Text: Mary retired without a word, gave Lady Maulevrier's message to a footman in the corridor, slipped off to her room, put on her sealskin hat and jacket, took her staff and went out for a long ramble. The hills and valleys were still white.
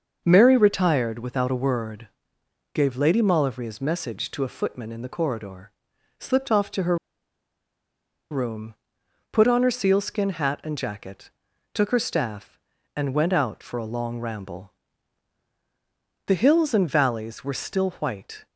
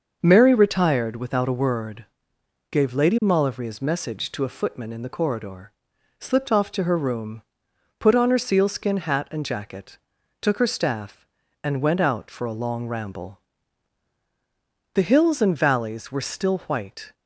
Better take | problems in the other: second | starts louder than the rest; until 1.2 s; 6.5 dB; also in the second // pauses between "her" and "room"; strong; at 6.9 s; 1.3 s long

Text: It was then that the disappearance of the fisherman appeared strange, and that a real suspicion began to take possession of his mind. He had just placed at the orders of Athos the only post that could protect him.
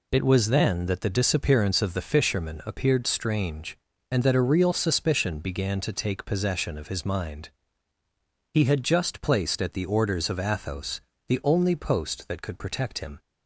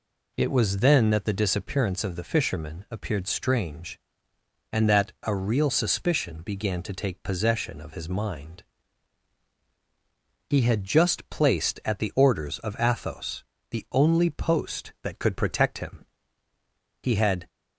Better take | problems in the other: first | pauses between "Athos" and "the"; slight; at 13.4 s; 0.26 s long; slight in the first // goes on to say "He had"; slight; from 17.0 s on; 0.46 s long

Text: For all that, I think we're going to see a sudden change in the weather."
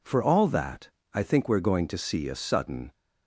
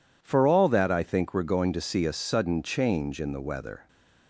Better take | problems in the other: second | stops before "change in the weather"; at 2.9 s

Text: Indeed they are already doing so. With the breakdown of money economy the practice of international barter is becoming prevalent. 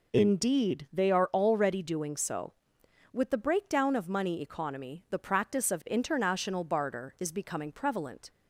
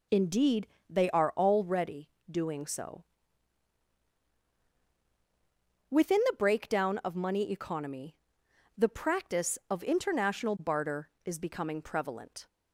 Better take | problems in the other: first | pauses between "Indeed" and "they"; slight; at 0.6 s; 0.22 s long // pauses between "already" and "doing"; slight; at 2.0 s; 0.22 s long // says "Within" for "With"; at 5.9 s // pauses between "economy" and "the"; noticeable; at 8.1 s; 0.62 s long

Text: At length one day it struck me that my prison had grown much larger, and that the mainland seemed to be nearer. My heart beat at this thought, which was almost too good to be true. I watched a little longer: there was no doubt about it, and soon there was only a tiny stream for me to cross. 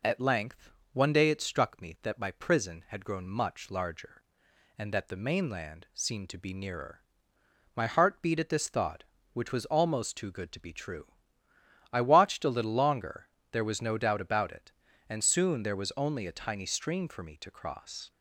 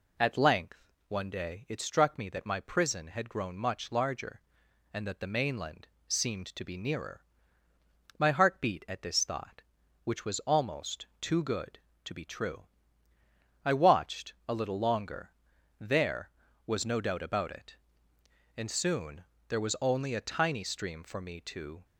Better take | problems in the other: first | pauses between "length" and "one"; slight; at 0.8 s; 0.28 s long; slight in the first // pauses between "mainland" and "seemed"; slight; at 5.8 s; 0.18 s long // pauses between "almost" and "too"; slight; at 11.0 s; 0.16 s long // pauses between "watched" and "a"; slight; at 14.3 s; 0.16 s long // pauses between "soon" and "there"; slight; at 19.2 s; 0.26 s long // stops before "cross"; at 21.8 s

